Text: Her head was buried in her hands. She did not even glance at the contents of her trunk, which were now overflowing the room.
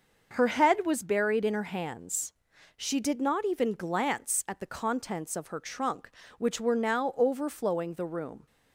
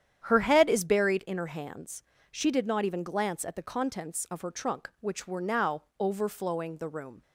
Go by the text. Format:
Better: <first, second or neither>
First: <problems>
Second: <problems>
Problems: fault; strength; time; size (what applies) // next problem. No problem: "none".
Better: first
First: starts louder than the rest; noticeable; until 1.3 s; 6 dB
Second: starts louder than the rest; strong; until 1.2 s; 9.5 dB // says "is" for "was"; at 0.6 s // pauses between "now" and "overflowing"; slight; at 5.8 s; 0.18 s long